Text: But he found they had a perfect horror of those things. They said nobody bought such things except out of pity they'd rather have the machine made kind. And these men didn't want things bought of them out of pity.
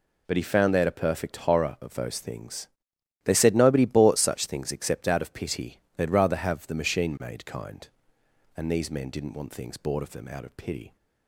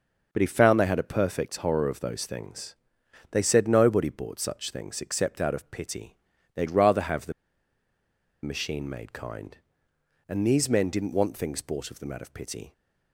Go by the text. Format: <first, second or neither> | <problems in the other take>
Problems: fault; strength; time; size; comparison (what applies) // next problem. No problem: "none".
first | starts louder than the rest; noticeable; until 1.3 s; 6 dB // pauses between "pity" and "they'd"; at 6.1 s; 0.38 s long; slight in the first // pauses between "the" and "machine"; at 7.3 s; 1.1 s long